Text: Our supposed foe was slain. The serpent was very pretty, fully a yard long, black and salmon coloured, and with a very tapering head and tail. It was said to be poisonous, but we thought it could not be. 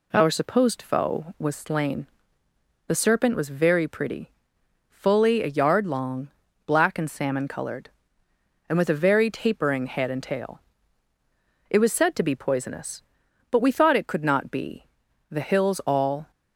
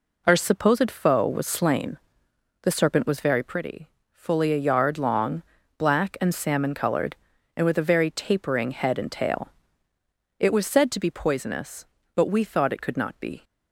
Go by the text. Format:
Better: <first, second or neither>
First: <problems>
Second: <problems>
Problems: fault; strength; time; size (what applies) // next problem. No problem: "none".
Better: second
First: goes on to say "The hills all"; noticeable; from 15.3 s on; 1.0 s long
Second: none